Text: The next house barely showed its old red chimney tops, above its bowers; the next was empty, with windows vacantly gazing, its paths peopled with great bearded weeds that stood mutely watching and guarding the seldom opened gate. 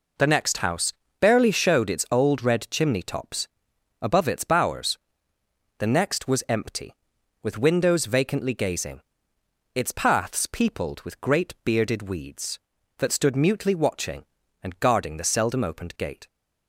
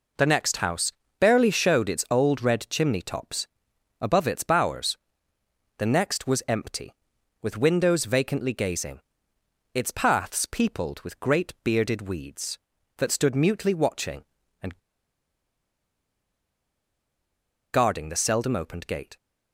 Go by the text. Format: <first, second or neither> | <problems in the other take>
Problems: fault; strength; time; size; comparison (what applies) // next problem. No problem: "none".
first | pauses between "house" and "barely"; slight; at 0.9 s; 0.28 s long; slight in the first // pauses between "and" and "guarding"; strong; at 14.7 s; 2.9 s long